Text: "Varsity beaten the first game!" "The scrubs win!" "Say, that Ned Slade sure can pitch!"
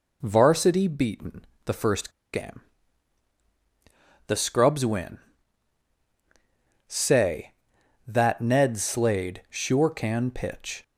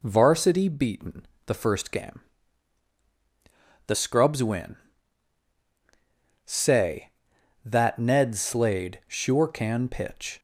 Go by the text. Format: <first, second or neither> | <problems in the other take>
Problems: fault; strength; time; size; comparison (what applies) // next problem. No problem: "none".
second | pauses between "beaten" and "the"; slight; at 1.4 s; 0.20 s long; slight in the second // pauses between "first" and "game"; slight; at 2.1 s; 0.21 s long